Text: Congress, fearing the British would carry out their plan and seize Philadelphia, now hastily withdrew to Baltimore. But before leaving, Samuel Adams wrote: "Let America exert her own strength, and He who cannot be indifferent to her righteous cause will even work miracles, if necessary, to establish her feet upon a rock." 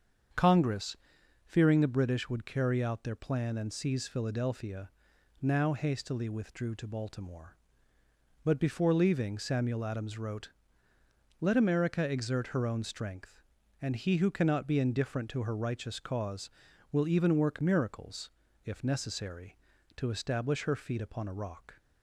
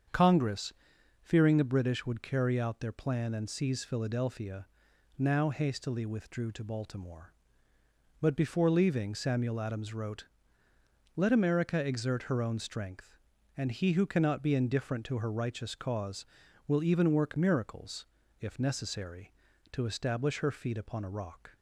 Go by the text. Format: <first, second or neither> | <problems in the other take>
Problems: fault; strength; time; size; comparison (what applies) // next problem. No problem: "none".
neither | starts louder than the rest; strong; the same in both